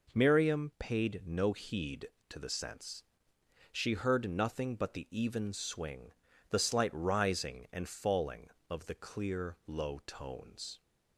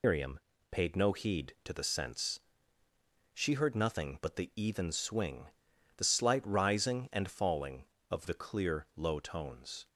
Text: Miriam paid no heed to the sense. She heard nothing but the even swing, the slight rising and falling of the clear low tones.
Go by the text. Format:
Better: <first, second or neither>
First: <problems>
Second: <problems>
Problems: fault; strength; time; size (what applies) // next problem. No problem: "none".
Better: first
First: none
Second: loses the start of "Miriam"; at 0.0 s; 145 ms // pauses between "Miriam" and "paid"; slight; at 0.3 s; 0.32 s long